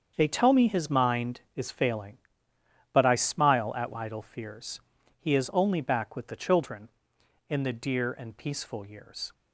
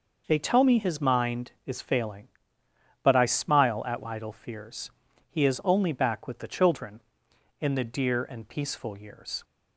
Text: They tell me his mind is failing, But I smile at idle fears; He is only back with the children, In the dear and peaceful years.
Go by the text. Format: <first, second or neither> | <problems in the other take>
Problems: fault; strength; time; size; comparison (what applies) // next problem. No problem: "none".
second | gets quieter; strong; throughout; 11.5 dB